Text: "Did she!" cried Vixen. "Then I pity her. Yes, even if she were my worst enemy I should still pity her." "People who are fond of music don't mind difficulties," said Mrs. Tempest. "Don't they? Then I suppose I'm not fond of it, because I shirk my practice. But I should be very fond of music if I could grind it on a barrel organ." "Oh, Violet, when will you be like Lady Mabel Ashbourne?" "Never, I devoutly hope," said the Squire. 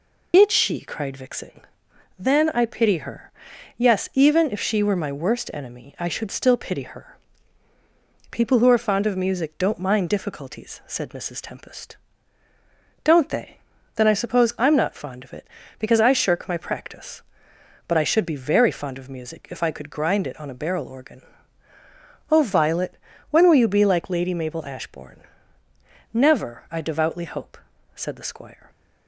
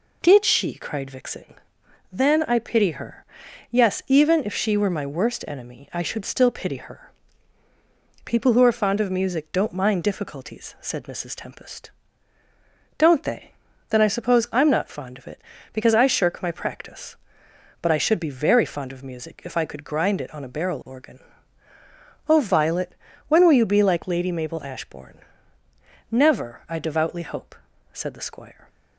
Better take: second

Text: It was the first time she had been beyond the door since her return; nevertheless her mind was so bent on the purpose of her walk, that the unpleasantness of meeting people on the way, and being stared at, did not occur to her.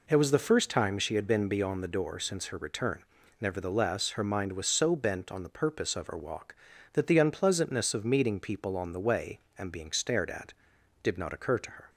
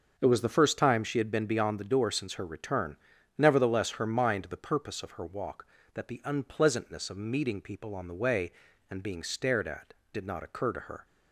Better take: first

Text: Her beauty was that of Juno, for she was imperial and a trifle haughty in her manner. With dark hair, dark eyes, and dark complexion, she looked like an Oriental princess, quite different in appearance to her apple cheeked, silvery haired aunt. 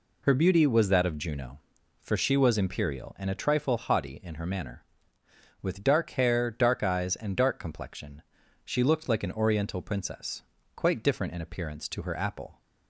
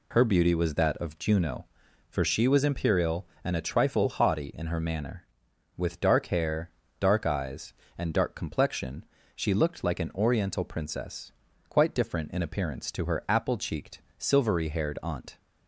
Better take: second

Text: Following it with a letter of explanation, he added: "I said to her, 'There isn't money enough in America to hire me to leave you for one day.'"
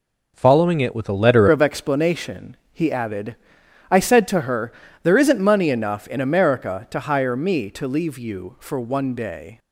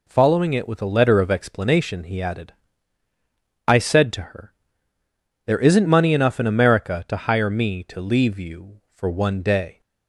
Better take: second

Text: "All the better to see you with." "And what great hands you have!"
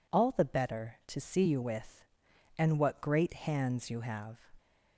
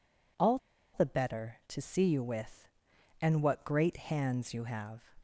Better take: first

